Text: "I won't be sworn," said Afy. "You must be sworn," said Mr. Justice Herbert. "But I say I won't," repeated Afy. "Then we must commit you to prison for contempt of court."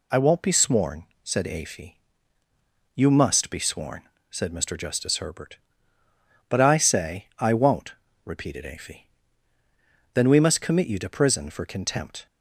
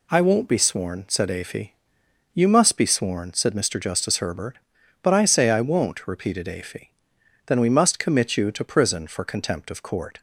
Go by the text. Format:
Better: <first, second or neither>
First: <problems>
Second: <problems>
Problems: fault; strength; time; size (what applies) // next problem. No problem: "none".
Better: second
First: stops before "of court"; at 12.2 s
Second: none